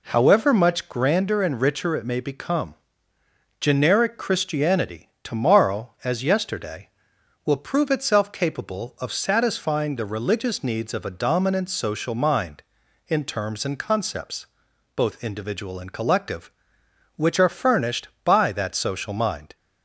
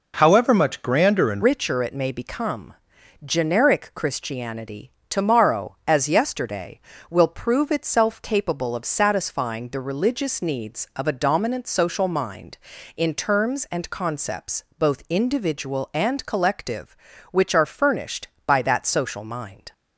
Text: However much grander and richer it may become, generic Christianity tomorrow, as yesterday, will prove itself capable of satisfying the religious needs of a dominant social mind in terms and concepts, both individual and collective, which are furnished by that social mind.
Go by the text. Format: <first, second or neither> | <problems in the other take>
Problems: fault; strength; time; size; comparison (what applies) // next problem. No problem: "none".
first | changes voice at "richer"; from 1.4 s on; 18.3 s long // pauses between "Christianity" and "tomorrow"; slight; at 4.9 s; 0.16 s long; slight in the first